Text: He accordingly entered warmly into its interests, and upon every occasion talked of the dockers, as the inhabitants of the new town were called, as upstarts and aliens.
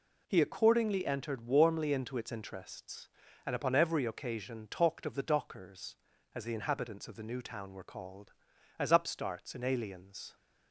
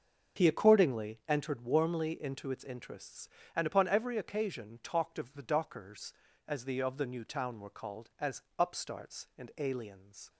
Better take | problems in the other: first | starts louder than the rest; until 1.4 s; 6 dB // skips "inhabitants"; at 6.7 s // pauses between "as" and "upstarts"; slight; at 8.4 s; 0.16 s long

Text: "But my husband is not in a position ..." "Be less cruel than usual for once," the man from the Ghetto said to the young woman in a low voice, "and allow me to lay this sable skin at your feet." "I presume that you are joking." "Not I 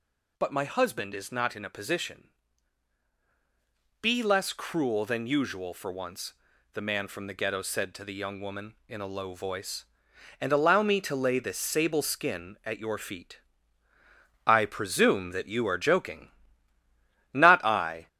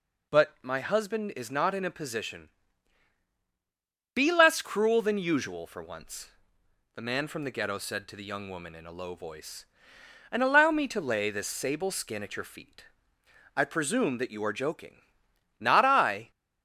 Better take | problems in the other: second | gets louder; strong; throughout; 14 dB

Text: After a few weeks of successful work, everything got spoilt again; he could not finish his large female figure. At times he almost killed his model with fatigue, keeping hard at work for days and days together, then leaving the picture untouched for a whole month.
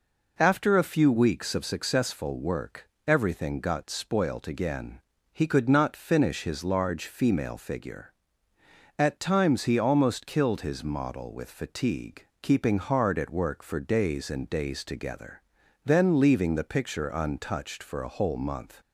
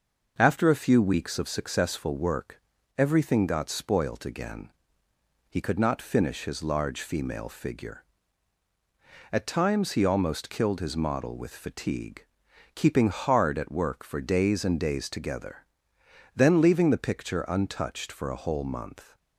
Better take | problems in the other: neither | none

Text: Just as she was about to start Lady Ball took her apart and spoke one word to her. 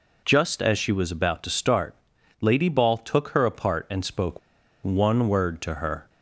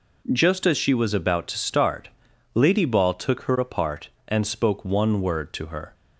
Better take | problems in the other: second | pauses between "start" and "Lady"; at 1.9 s; 0.44 s long; also in the second // pauses between "spoke" and "one"; at 4.3 s; 0.44 s long

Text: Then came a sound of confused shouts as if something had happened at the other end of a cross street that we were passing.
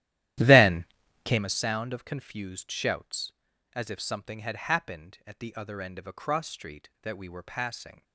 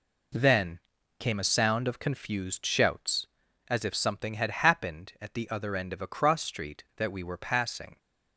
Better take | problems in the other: second | starts louder than the rest; strong; until 1.6 s; 13 dB // pauses between "Then" and "came"; at 0.8 s; 0.40 s long; also in the second

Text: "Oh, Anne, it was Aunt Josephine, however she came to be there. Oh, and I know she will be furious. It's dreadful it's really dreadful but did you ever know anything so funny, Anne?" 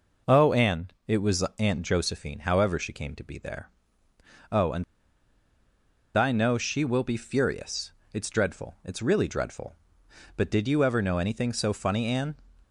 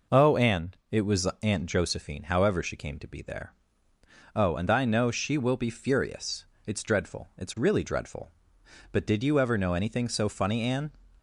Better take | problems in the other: second | pauses between "and" and "I"; strong; at 4.8 s; 1.3 s long

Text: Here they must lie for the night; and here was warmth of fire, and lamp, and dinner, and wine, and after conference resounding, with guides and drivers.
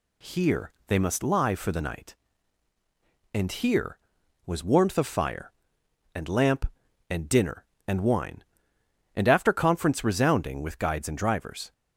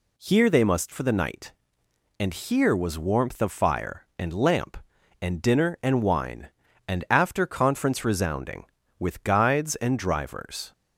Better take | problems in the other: first | skips "lie"; at 0.9 s

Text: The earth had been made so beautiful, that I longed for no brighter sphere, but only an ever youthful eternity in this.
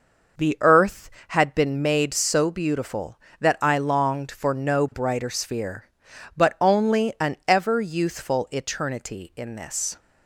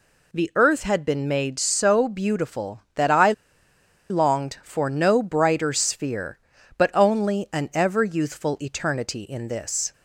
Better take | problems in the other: first | pauses between "I" and "longed"; noticeable; at 3.3 s; 0.76 s long

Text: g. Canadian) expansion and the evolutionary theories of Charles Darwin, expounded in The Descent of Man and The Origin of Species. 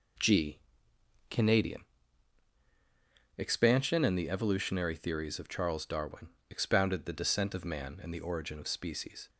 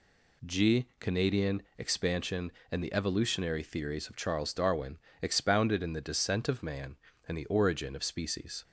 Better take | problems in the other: second | skips "in"; at 7.0 s

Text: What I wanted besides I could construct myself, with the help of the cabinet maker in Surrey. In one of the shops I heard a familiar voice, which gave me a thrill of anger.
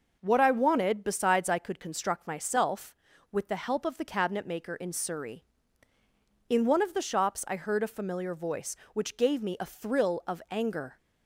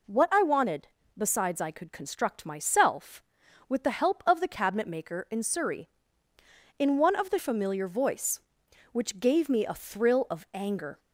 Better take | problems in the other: first | pauses between "wanted" and "besides"; slight; at 0.8 s; 0.28 s long // skips "shops I heard a"; at 7.3 s

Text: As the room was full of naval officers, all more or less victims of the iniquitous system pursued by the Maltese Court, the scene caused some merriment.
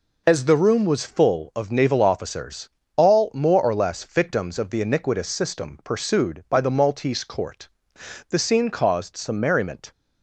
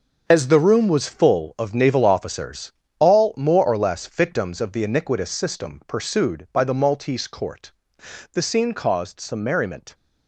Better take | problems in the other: first | gets quieter; strong; throughout; 10 dB

